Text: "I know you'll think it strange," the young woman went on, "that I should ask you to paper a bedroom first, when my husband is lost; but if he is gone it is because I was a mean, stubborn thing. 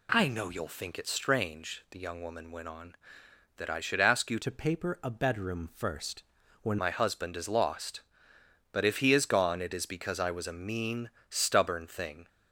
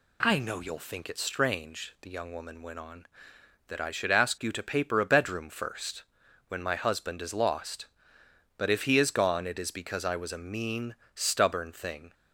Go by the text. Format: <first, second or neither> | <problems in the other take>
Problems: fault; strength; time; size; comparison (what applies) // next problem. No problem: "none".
second | changes voice from "to" to "when"; from 4.4 to 6.7 s; 2.3 s long